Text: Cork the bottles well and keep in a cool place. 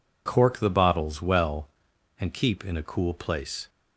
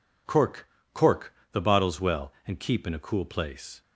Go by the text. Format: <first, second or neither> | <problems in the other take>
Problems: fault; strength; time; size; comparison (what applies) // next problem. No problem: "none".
first | says "Cork" twice; at 0.9 s